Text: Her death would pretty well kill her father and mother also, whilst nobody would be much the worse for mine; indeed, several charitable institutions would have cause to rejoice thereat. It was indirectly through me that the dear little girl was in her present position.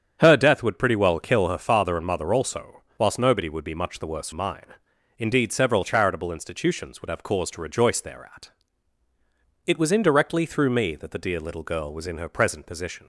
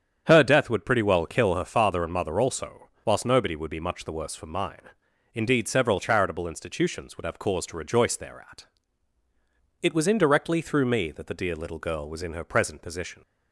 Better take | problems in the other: second | starts louder than the rest; strong; until 1.2 s; 8 dB; strong in the second // skips "for"; at 4.3 s

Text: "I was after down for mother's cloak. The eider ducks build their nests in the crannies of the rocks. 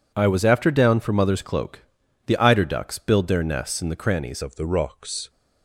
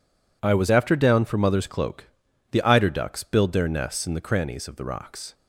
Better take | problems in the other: second | changes voice at "of"; from 4.4 s on; 0.8 s long

